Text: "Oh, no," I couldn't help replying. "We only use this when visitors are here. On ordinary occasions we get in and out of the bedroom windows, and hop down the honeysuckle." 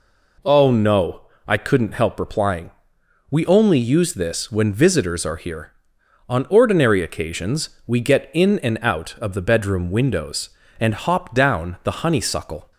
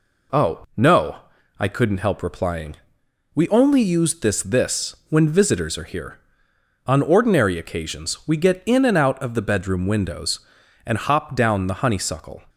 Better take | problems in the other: first | says "this" twice; at 4.4 s

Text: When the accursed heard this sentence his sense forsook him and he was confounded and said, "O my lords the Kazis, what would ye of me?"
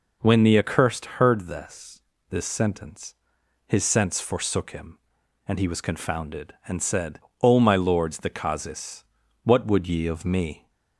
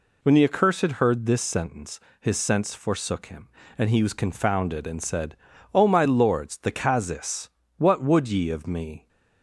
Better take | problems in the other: second | pauses between "accursed" and "heard"; slight; at 1.0 s; 0.16 s long // says "this" twice; at 2.3 s // pauses between "sentence" and "his"; noticeable; at 3.1 s; 0.54 s long; slight in the second

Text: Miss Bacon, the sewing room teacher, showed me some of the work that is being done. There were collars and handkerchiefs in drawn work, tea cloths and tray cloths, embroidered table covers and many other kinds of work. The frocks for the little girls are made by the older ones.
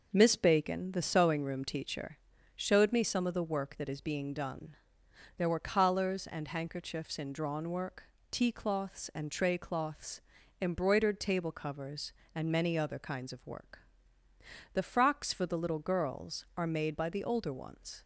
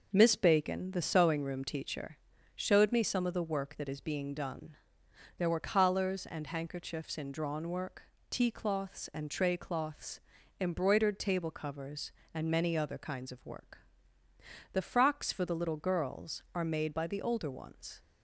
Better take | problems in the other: neither | none

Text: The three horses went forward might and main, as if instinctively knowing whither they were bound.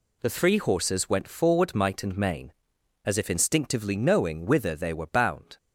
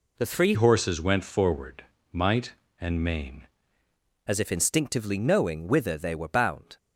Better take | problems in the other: first | changes voice from "horses" to "main"; from 0.5 to 3.4 s; 2.9 s long // pauses between "forward" and "might"; slight; at 1.8 s; 0.28 s long

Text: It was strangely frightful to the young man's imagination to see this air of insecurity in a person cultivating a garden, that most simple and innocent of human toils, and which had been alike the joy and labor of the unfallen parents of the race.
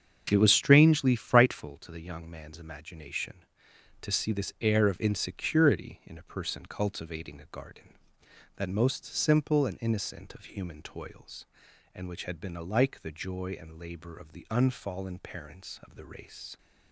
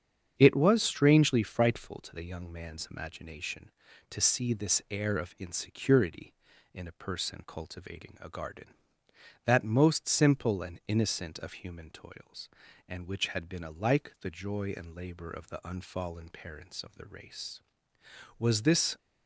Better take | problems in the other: first | starts louder than the rest; strong; until 1.3 s; 7.5 dB; strong in the first // goes on to say "Was this"; from 18.3 s on; 0.58 s long

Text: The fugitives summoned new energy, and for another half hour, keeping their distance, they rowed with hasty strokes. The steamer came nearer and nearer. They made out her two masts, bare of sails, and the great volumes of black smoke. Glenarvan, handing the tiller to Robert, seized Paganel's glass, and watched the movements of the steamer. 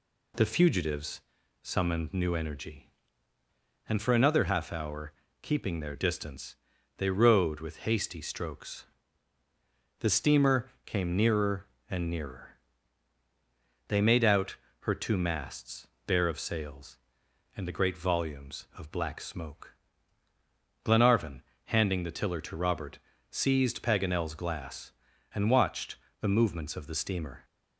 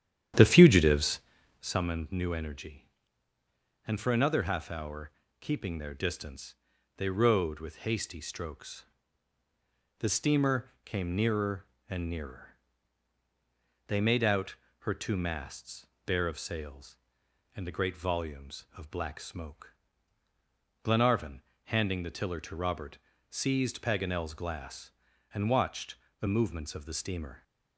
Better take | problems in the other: first | starts louder than the rest; strong; until 1.8 s; 10 dB // pauses between "fugitives" and "summoned"; at 1.1 s; 0.42 s long; also in the first // pauses between "steamer" and "came"; slight; at 10.6 s; 0.18 s long; slight in the first // pauses between "out" and "her"; slight; at 14.5 s; 0.24 s long; slight in the first // pauses between "watched" and "the"; slight; at 25.9 s; 0.26 s long; slight in the first

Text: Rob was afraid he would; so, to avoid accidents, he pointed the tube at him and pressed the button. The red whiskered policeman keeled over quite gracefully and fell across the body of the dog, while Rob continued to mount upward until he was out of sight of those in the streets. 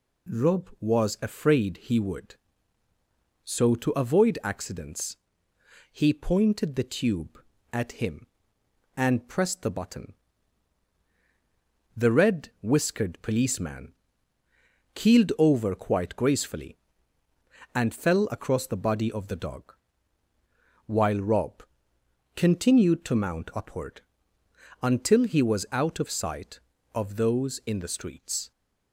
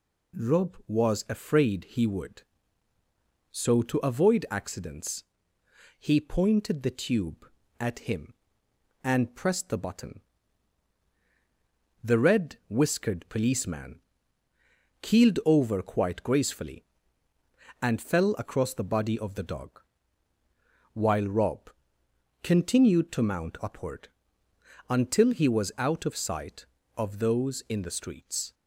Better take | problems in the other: neither | pauses between "policeman" and "keeled"; the same in both // pauses between "Rob" and "continued"; noticeable; the same in both // pauses between "upward" and "until"; noticeable; the same in both

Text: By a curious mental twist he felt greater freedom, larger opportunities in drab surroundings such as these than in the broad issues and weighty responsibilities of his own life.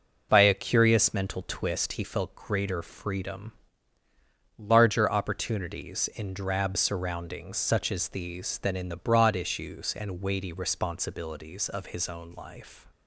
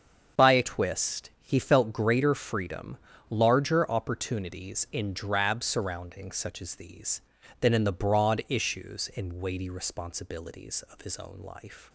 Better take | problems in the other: first | starts louder than the rest; until 1.5 s; 7 dB // skips "curious mental"; at 0.6 s

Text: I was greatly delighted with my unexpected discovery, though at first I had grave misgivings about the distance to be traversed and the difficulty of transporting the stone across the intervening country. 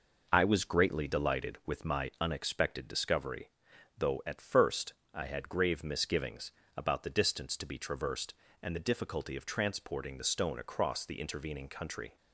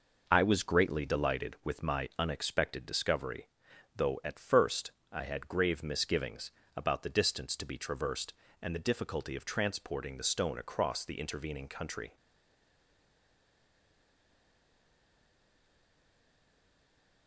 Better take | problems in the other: first | pauses between "first" and "I"; slight; at 4.9 s; 0.22 s long; slight in the first // pauses between "misgivings" and "about"; slight; at 6.5 s; 0.26 s long; slight in the first // stays silent after the last word; strong; from 12.1 s on; 5.1 s long

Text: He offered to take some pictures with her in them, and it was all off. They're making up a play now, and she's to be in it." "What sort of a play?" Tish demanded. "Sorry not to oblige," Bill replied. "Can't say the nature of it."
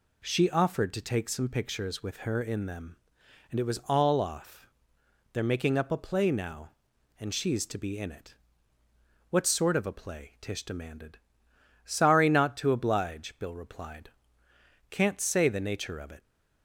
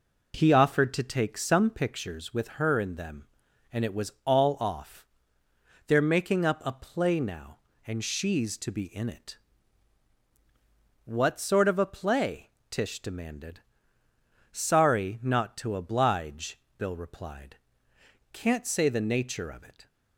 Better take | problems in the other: second | says "She" for "He"; at 0.2 s

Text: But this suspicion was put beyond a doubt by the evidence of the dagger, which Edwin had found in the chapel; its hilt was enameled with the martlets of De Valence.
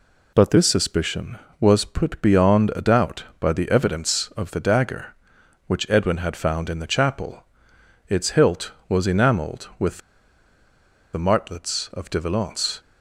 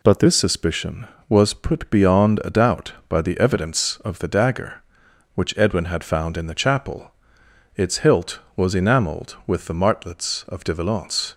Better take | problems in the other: second | pauses between "with" and "the"; at 9.9 s; 1.1 s long

